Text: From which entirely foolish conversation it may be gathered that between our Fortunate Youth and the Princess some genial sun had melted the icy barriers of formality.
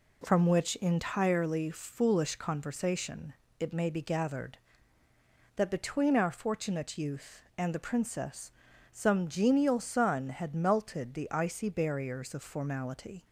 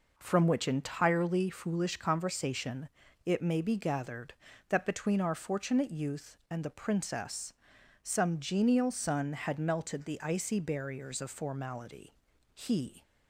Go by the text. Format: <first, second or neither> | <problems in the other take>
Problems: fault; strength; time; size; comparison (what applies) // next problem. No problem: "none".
first | pauses between "conversation" and "it"; slight; at 2.8 s; 0.36 s long; slight in the first // pauses between "Princess" and "some"; noticeable; at 7.5 s; 0.50 s long; also in the first // goes on to say "He"; slight; from 12.5 s on; 0.48 s long